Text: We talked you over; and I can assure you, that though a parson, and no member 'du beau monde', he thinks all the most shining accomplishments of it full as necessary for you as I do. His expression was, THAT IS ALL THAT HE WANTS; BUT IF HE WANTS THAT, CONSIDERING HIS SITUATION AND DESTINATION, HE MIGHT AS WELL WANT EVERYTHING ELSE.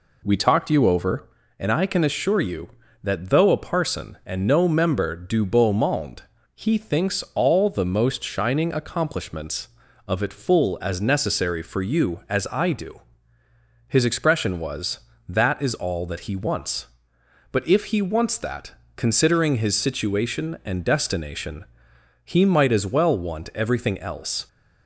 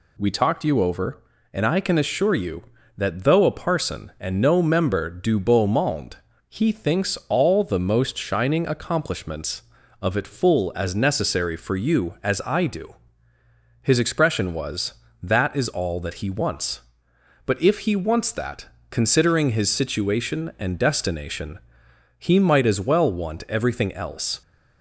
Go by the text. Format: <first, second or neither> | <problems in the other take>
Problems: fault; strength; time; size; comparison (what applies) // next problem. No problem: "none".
second | starts louder than the rest; slight; until 1.5 s; 3 dB